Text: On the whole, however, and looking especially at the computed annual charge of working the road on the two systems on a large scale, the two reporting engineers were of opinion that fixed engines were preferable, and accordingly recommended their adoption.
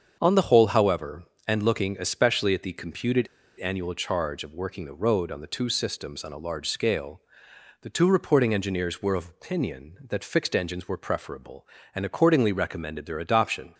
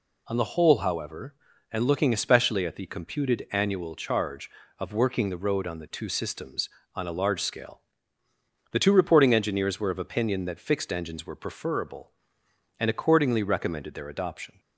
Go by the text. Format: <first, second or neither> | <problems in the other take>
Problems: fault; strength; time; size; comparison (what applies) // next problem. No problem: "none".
second | starts louder than the rest; until 1.2 s; 7 dB // pauses between "computed" and "annual"; slight; at 3.2 s; 0.30 s long